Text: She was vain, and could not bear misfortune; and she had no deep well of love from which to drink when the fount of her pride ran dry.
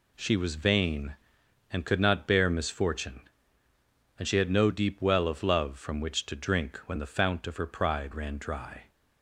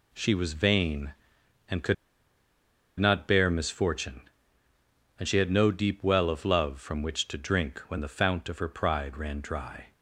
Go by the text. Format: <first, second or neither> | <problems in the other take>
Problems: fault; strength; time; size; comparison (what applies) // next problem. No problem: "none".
first | pauses between "could" and "not"; at 1.9 s; 1.0 s long